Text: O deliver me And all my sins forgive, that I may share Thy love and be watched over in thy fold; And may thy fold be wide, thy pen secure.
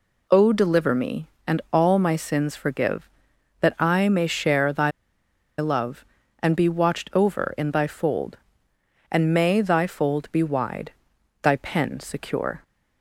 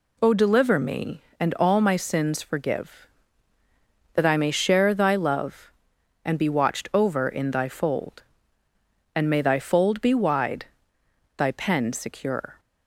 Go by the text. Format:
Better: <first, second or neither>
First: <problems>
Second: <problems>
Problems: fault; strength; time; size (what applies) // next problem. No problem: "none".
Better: second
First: pauses between "Thy" and "love"; noticeable; at 4.9 s; 0.67 s long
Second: none